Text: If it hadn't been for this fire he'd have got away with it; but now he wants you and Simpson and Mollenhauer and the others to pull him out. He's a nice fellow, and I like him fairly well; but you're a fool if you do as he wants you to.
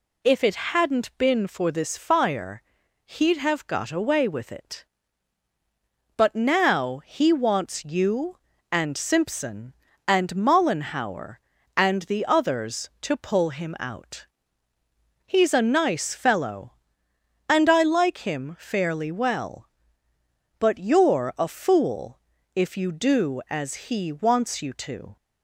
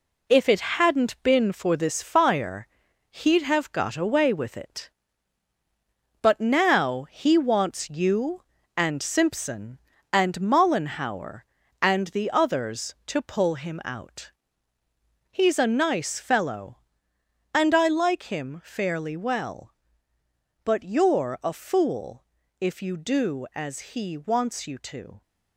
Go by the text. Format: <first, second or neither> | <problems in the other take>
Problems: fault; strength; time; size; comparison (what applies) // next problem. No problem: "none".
first | gets quieter; throughout; 7 dB // pauses between "fire" and "he'd"; at 2.6 s; 0.44 s long; also in the first // pauses between "fool" and "if"; slight; at 22.2 s; 0.34 s long; slight in the first